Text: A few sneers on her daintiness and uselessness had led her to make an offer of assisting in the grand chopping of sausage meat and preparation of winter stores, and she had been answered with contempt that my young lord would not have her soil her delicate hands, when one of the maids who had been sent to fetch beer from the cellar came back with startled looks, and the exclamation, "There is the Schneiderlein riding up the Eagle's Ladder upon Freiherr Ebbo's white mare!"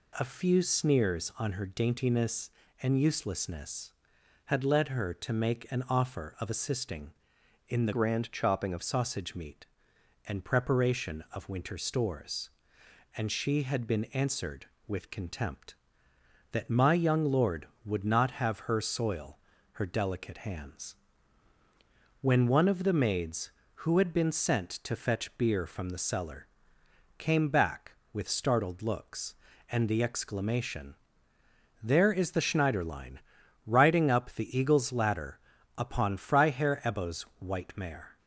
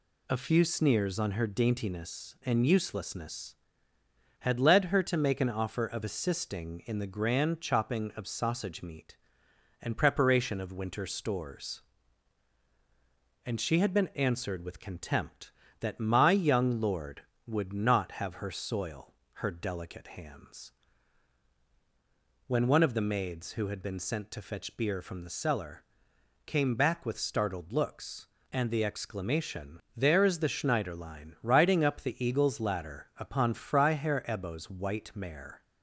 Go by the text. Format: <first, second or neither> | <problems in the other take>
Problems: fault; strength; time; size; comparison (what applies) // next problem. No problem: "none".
second | changes voice from "grand" to "of"; from 7.9 to 8.8 s; 0.9 s long // pauses between "soil" and "her"; at 19.3 s; 0.40 s long; slight in the second // pauses between "cellar" and "came"; noticeable; at 26.4 s; 0.72 s long; noticeable in the second // pauses between "Schneiderlein" and "riding"; noticeable; at 33.1 s; 0.46 s long // pauses between "Ladder" and "upon"; at 35.3 s; 0.38 s long // pauses between "Ebbo's" and "white"; slight; at 37.2 s; 0.18 s long